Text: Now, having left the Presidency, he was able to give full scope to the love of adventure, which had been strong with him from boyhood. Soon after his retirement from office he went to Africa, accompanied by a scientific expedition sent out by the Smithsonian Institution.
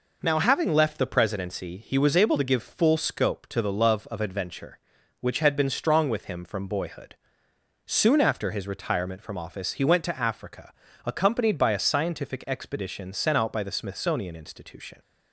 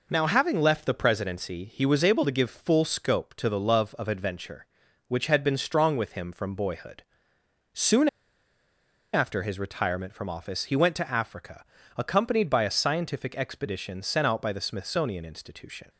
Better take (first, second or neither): first